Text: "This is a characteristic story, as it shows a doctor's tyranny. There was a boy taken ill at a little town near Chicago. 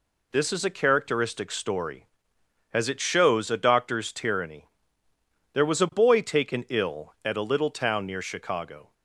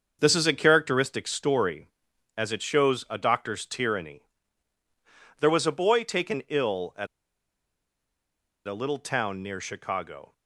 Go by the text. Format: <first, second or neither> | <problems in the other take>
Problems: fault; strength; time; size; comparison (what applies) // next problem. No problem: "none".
first | starts louder than the rest; until 1.2 s; 6.5 dB // pauses between "at" and "a"; strong; at 7.0 s; 1.5 s long